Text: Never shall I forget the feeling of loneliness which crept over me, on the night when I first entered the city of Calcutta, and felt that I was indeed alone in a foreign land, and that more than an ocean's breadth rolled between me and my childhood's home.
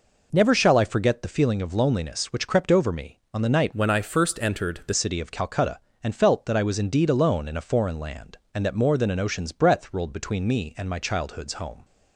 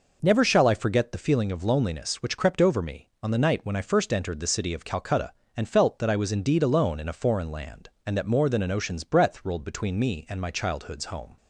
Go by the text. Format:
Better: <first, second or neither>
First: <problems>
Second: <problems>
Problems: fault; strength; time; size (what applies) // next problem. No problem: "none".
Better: second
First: changes voice from "when" to "the"; from 3.7 to 4.9 s; 1.2 s long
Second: none